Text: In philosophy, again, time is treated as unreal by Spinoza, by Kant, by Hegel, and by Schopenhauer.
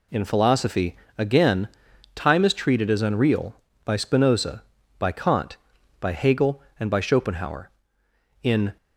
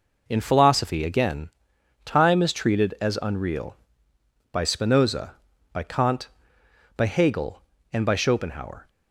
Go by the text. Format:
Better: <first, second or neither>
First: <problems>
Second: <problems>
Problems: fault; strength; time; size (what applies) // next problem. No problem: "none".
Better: second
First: goes on to say "In"; slight; from 8.4 s on; 0.34 s long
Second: none